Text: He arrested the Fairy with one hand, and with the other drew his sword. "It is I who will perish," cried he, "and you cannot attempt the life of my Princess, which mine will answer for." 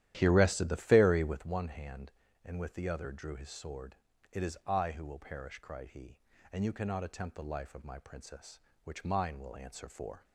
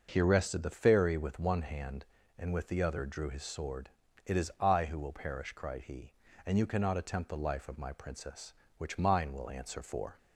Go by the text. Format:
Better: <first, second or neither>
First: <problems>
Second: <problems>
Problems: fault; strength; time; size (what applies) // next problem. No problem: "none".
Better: second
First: starts louder than the rest; strong; until 1.5 s; 12 dB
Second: none